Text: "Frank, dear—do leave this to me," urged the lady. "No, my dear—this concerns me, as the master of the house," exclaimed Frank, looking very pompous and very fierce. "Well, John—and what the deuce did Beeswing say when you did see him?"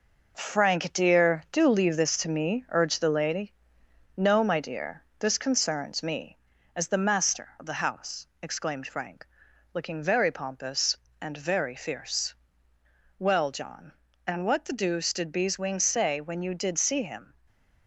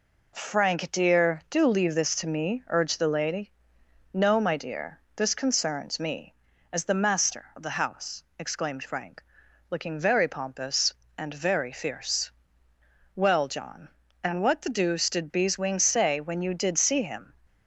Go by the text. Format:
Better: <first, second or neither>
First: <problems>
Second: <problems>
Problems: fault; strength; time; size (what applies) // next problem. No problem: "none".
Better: second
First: gets quieter; noticeable; throughout; 5 dB // stays silent after the last word; slight; from 17.3 s on; 0.5 s long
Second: none